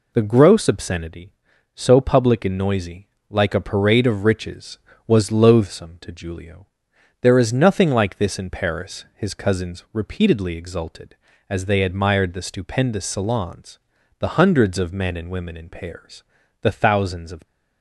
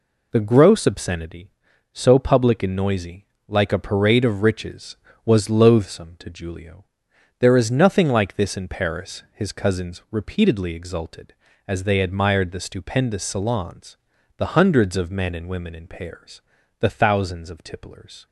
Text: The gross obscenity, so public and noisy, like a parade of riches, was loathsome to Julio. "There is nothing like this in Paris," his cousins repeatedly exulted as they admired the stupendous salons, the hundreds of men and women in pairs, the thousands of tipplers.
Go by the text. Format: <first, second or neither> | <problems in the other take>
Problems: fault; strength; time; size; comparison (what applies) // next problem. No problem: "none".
second | stops before "tipplers"; at 17.4 s